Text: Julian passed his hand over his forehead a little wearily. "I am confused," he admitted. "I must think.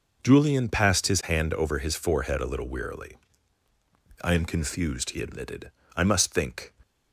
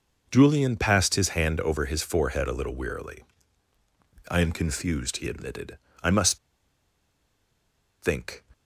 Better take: first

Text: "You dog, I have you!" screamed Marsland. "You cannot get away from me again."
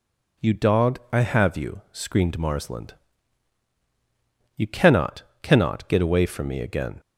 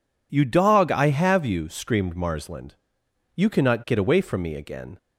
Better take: second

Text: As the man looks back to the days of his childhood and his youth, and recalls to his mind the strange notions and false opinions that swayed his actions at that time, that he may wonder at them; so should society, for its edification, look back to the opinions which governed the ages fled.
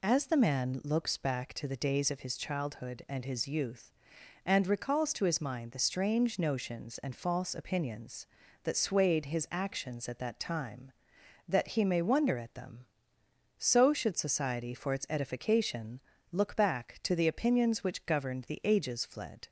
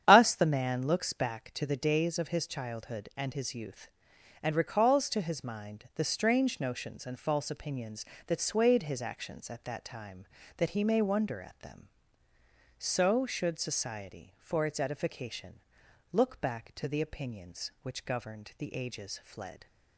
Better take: first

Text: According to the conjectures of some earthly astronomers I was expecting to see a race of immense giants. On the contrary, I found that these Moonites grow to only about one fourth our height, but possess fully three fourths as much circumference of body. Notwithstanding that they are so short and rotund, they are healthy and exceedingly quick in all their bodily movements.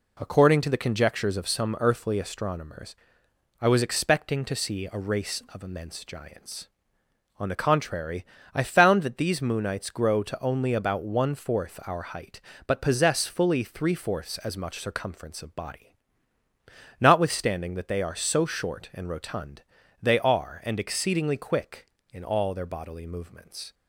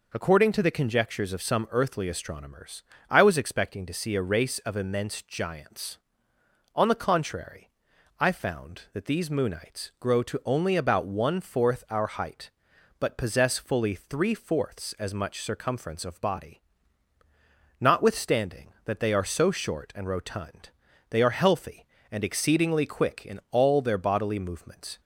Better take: second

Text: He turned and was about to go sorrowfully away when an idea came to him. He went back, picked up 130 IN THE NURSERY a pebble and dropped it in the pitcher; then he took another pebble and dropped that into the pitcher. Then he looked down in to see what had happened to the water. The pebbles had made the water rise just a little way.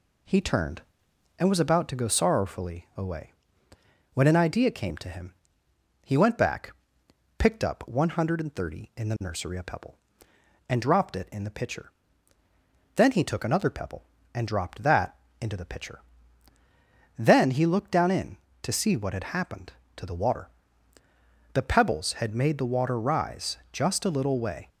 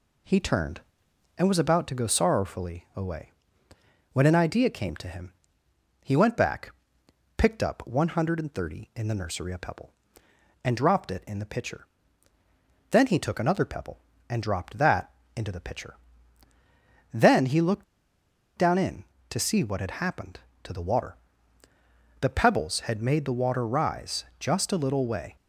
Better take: first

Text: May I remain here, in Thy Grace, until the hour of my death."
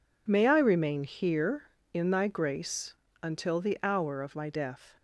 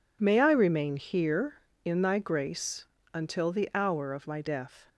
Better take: neither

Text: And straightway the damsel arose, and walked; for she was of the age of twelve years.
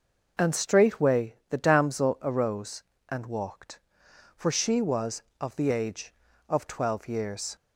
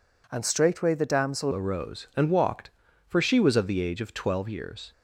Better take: first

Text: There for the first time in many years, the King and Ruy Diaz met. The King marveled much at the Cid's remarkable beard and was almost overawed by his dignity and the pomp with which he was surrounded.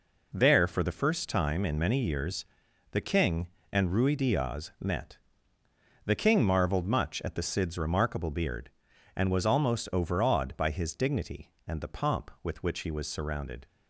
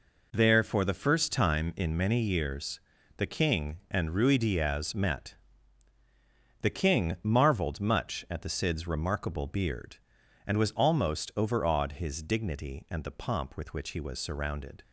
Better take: first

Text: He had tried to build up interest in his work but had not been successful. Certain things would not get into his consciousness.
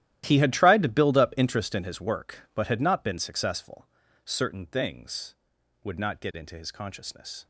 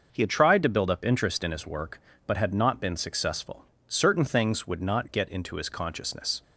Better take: second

